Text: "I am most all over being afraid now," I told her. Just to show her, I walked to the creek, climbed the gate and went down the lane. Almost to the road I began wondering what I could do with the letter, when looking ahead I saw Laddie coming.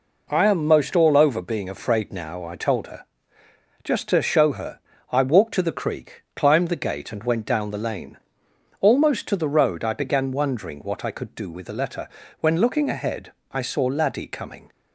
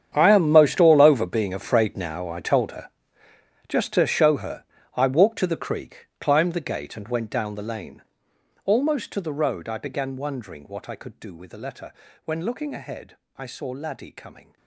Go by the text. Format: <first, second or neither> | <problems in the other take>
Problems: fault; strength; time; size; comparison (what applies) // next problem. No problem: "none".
first | gets quieter; strong; throughout; 17.5 dB // pauses between "ahead" and "I"; slight; at 13.1 s; 0.20 s long; slight in the first